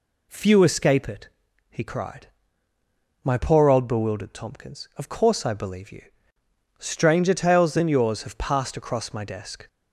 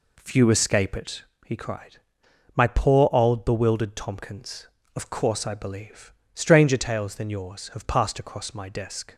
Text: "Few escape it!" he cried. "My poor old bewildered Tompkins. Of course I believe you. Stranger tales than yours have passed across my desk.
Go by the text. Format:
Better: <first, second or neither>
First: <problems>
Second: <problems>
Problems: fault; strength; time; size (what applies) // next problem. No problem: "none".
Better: first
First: none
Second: skips "you"; at 6.2 s